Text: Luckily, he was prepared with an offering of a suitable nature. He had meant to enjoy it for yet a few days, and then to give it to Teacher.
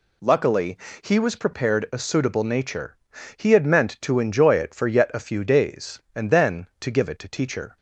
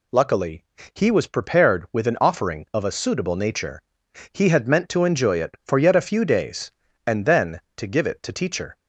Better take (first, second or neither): second